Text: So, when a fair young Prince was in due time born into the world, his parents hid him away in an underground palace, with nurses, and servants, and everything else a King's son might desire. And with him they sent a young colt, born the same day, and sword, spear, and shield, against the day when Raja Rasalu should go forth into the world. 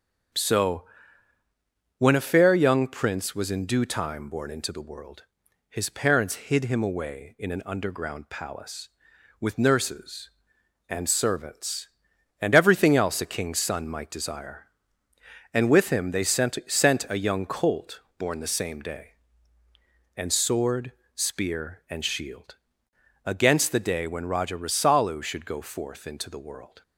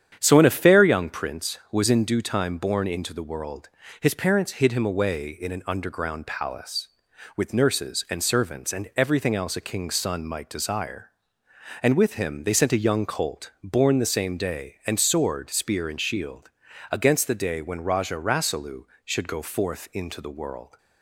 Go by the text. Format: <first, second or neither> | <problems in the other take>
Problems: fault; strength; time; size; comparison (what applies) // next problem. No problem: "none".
second | starts louder than the rest; strong; until 2.4 s; 7.5 dB; strong in the second // says "sent" twice; at 16.6 s